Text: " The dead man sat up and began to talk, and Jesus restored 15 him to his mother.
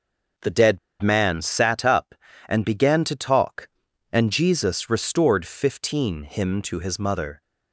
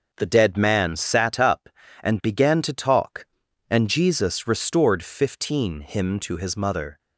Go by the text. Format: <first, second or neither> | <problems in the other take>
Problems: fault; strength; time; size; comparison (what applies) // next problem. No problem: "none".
second | starts louder than the rest; until 1.6 s; 6 dB // pauses between "dead" and "man"; slight; at 0.7 s; 0.25 s long